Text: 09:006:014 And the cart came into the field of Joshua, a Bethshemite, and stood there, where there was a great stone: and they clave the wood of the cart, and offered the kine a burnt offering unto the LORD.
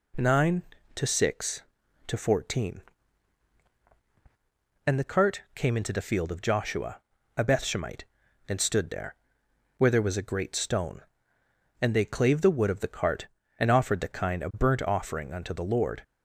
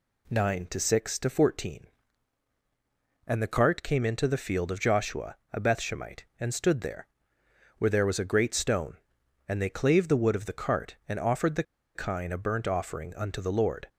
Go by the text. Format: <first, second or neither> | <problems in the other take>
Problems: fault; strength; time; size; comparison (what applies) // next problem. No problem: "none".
first | pauses between "the" and "kine"; slight; at 11.6 s; 0.33 s long